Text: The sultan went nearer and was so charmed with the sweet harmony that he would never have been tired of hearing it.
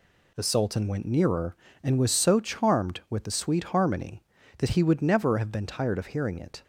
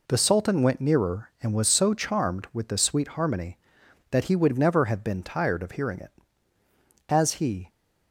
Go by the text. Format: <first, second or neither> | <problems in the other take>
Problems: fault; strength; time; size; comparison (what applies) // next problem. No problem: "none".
first | goes on to say "As he"; from 7.0 s on; 0.60 s long